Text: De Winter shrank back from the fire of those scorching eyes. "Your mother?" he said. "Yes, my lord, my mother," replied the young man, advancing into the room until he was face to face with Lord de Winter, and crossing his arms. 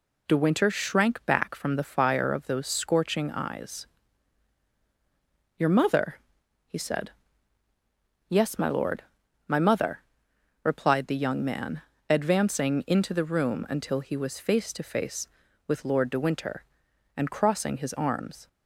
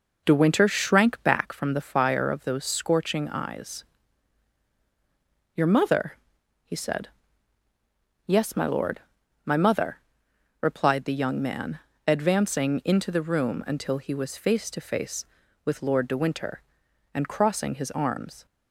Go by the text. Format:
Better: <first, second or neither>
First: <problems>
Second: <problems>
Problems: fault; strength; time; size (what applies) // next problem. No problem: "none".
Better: first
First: none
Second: starts louder than the rest; noticeable; until 1.4 s; 4.5 dB